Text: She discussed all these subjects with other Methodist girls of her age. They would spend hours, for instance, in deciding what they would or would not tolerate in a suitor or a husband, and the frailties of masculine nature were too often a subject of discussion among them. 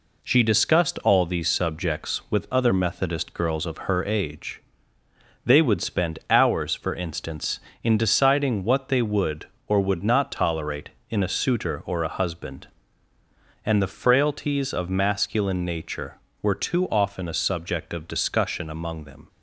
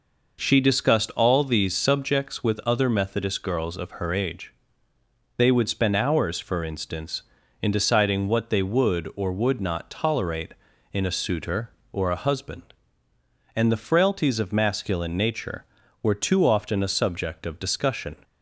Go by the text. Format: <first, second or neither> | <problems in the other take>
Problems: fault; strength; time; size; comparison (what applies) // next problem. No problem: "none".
first | stops before "among them"; at 18.2 s